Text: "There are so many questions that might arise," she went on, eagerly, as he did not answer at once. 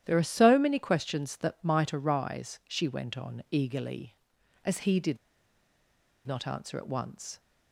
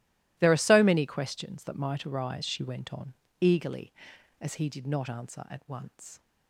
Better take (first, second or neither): second